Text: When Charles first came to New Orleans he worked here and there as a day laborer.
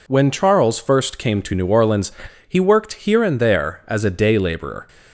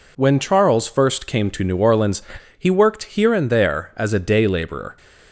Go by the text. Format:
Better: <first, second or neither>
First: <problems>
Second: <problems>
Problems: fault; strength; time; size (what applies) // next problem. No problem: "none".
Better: neither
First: pauses between "Orleans" and "he"; slight; at 2.1 s; 0.36 s long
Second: pauses between "Orleans" and "he"; slight; at 2.2 s; 0.36 s long